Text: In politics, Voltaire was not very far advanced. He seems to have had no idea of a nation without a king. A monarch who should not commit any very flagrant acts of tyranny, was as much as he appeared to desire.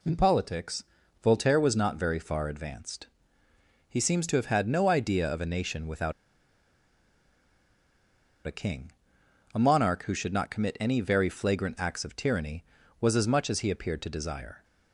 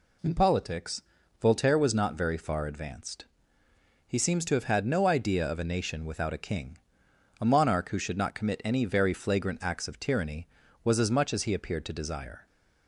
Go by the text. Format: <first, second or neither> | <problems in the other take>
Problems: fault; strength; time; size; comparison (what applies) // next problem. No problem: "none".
second | pauses between "without" and "a"; strong; at 6.1 s; 2.3 s long